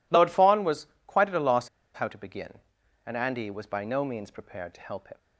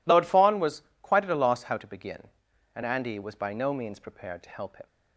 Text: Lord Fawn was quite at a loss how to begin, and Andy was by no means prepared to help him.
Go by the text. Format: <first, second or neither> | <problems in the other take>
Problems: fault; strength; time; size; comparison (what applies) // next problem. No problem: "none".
second | pauses between "was" and "quite"; slight; at 0.8 s; 0.20 s long; slight in the second // pauses between "loss" and "how"; slight; at 1.6 s; 0.26 s long